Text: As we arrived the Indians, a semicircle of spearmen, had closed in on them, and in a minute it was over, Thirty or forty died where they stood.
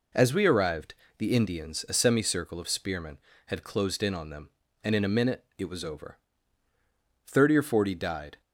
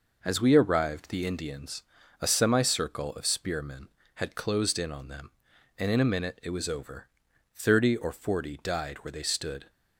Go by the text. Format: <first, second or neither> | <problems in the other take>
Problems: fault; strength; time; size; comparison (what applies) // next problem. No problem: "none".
second | pauses between "arrived" and "the"; slight; at 0.9 s; 0.24 s long // stops before "where they stood"; at 8.4 s